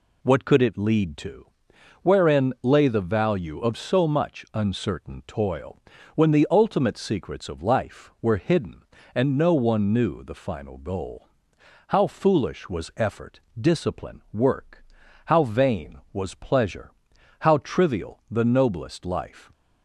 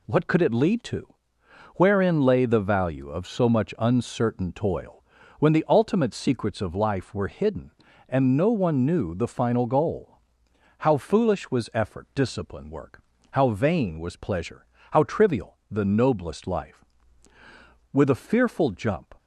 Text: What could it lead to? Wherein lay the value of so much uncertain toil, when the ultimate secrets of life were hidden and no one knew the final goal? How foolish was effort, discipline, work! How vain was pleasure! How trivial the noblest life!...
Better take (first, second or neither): first